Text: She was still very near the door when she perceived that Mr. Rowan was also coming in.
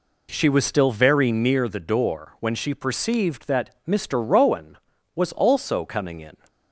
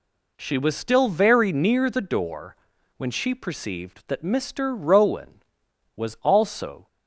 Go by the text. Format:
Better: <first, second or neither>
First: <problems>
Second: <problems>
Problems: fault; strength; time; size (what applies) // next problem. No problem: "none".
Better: first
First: none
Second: pauses between "door" and "when"; at 2.5 s; 0.42 s long // stops before "coming in"; at 6.8 s